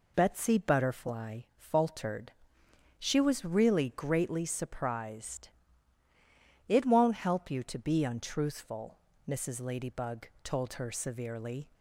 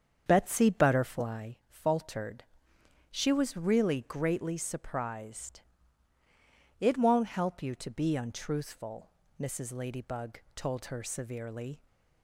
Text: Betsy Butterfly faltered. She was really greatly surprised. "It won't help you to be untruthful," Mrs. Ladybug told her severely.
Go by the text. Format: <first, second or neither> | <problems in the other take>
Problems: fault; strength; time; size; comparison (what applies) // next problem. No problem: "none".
first | starts louder than the rest; strong; until 1.4 s; 7.5 dB // pauses between "Butterfly" and "faltered"; slight; at 1.5 s; 0.16 s long; slight in the first